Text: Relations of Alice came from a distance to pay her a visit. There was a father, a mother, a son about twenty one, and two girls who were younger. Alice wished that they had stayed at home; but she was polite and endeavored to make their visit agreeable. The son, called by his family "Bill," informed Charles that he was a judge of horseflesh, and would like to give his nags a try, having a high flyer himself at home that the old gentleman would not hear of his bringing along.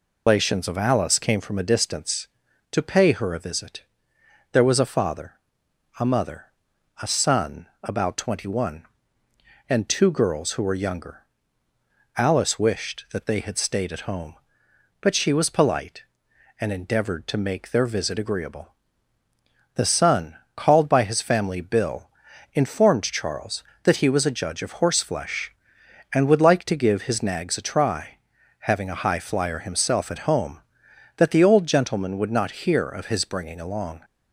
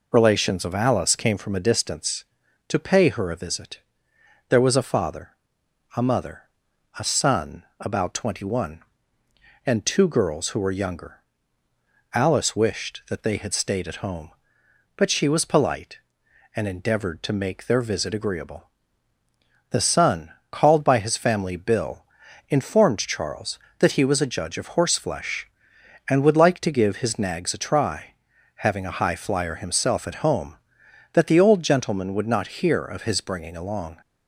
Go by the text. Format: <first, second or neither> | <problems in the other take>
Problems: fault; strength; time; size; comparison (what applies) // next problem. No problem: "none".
second | loses the start of "Relations"; at 0.2 s; 105 ms // pauses between "son" and "about"; slight; at 7.6 s; 0.16 s long; slight in the second